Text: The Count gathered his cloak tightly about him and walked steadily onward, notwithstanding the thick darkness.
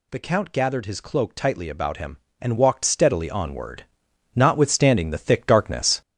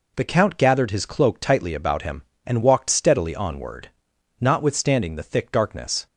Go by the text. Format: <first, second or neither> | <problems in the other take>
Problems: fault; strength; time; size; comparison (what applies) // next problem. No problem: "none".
second | gets louder; throughout; 6 dB